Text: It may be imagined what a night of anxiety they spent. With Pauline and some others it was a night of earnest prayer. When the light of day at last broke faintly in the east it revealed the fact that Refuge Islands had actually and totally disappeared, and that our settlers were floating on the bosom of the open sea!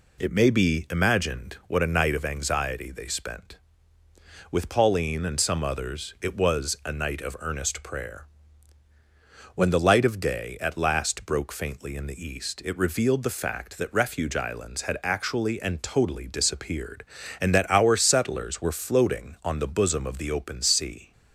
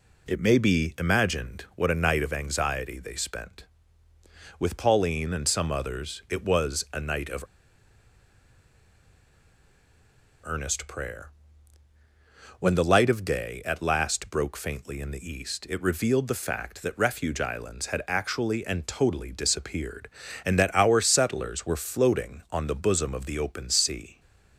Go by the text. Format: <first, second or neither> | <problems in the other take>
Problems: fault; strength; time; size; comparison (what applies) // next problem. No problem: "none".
first | pauses between "of" and "earnest"; strong; at 7.4 s; 2.9 s long